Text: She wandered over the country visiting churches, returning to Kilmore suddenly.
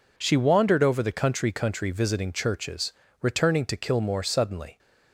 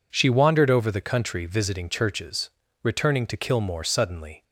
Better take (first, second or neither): second